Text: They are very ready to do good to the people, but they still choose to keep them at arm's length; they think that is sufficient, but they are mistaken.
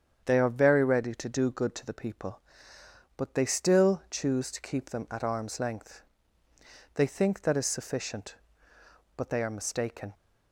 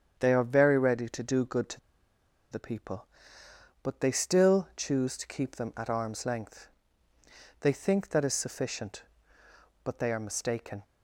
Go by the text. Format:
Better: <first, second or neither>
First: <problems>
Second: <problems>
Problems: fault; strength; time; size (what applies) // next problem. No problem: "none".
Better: first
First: starts louder than the rest; strong; until 1.2 s; 8 dB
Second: starts louder than the rest; strong; until 1.2 s; 8 dB // pauses between "to" and "the"; noticeable; at 1.7 s; 0.72 s long